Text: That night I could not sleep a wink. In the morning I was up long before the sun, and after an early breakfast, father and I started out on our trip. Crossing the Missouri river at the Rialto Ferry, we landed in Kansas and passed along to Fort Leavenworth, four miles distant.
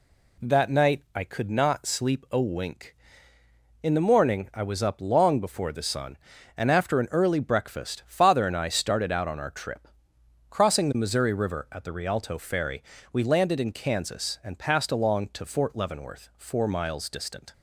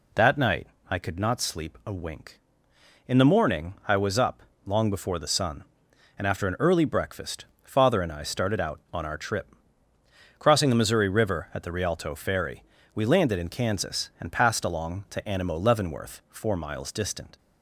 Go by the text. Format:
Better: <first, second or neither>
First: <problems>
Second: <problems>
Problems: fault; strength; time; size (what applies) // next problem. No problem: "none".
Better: first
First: none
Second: pauses between "night" and "I"; slight; at 0.6 s; 0.22 s long // pauses between "up" and "long"; slight; at 4.4 s; 0.22 s long // says "Animo" for "Fort"; at 15.2 s